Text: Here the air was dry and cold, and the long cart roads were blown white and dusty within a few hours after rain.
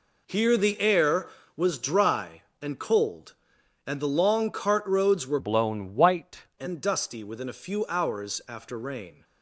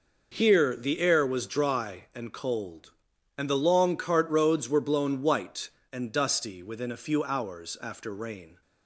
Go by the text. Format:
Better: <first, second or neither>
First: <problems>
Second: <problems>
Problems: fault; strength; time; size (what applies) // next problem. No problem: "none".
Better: second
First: changes voice from "blown" to "white"; from 5.3 to 6.4 s; 1.1 s long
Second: none